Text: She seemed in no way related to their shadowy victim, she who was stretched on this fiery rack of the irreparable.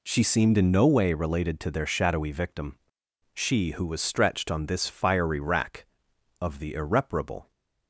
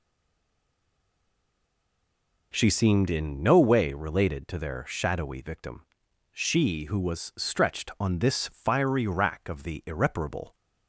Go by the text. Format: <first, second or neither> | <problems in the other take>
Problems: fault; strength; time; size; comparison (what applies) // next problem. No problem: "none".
first | stays silent before the first word; until 2.5 s; 2.5 s long